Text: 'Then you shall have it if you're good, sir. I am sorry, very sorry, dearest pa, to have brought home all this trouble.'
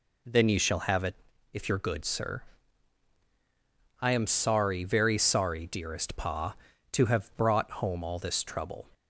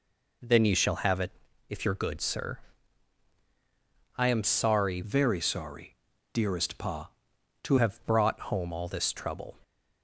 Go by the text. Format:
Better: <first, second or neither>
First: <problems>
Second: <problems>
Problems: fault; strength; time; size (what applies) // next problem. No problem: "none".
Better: first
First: pauses between "it" and "if"; at 1.1 s; 0.38 s long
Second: pauses between "it" and "if"; at 1.3 s; 0.38 s long // changes voice from "very" to "to"; from 5.0 to 7.7 s; 2.7 s long